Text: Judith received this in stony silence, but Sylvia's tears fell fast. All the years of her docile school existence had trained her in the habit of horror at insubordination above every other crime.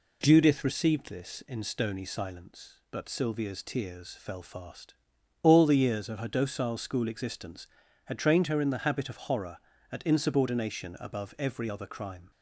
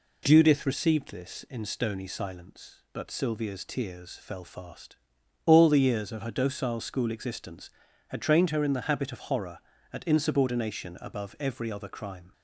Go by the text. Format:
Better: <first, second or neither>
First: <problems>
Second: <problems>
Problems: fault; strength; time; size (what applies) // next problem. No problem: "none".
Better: neither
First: none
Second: none